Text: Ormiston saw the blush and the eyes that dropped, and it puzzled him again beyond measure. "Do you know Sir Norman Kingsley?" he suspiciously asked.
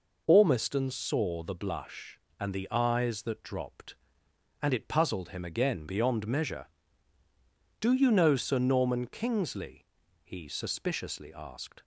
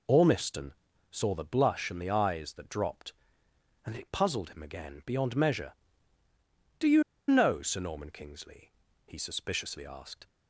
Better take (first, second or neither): first